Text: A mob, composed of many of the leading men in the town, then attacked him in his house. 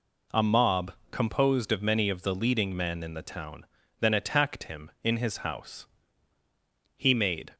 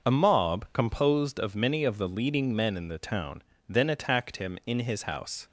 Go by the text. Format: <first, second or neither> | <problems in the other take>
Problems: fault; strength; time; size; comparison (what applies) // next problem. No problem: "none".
second | goes on to say "He made"; from 6.9 s on; 0.56 s long